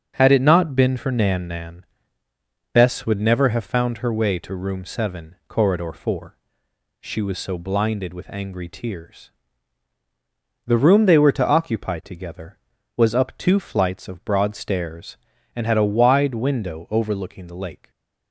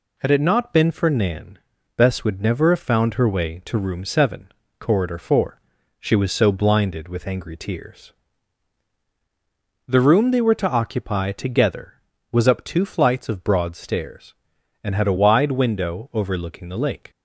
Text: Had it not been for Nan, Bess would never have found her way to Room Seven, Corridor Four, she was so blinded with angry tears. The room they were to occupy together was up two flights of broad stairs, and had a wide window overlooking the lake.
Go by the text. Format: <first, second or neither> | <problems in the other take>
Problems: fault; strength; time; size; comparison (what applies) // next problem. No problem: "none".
second | starts louder than the rest; until 1.1 s; 7 dB // says "Nan" twice; at 1.4 s